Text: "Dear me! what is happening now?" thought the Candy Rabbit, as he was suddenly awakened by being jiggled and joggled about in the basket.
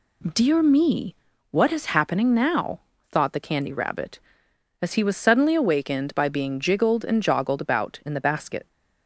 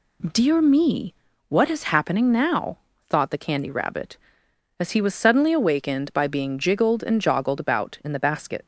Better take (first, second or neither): neither